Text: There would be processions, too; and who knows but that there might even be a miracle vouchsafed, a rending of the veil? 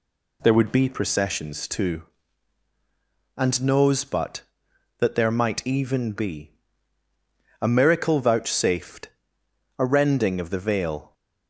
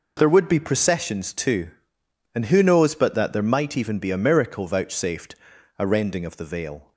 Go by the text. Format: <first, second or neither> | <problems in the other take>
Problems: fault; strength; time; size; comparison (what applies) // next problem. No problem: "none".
second | skips "who"; at 3.6 s // pauses between "be" and "a"; at 6.5 s; 1.0 s long